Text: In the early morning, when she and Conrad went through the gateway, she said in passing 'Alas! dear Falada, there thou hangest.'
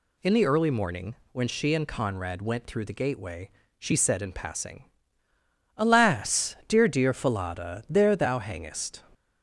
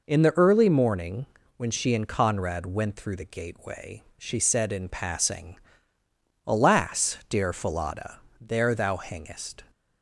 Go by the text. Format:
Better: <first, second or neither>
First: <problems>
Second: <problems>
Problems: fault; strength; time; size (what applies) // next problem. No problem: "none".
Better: second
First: pauses between "passing" and "Alas"; noticeable; at 4.8 s; 0.90 s long // says "dear" twice; at 6.8 s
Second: pauses between "passing" and "Alas"; noticeable; at 5.5 s; 0.90 s long